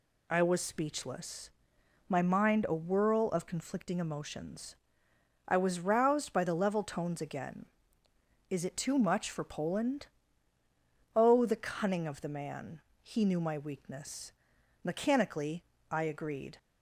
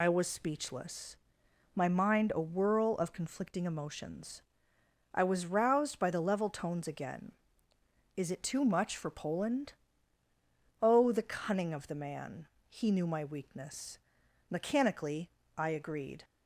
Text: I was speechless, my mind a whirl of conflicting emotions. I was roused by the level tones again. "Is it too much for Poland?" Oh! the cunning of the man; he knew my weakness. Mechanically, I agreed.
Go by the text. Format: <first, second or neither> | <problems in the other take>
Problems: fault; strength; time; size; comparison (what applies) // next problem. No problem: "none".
first | loses the start of "I"; at 0.0 s; 45 ms